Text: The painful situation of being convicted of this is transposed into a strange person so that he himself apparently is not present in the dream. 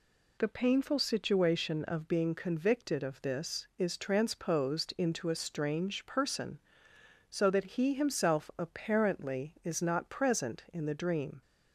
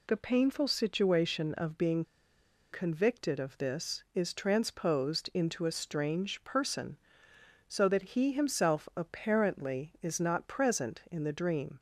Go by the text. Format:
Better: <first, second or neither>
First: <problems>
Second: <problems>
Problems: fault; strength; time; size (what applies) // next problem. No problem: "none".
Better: first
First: none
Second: pauses between "being" and "convicted"; noticeable; at 2.0 s; 0.69 s long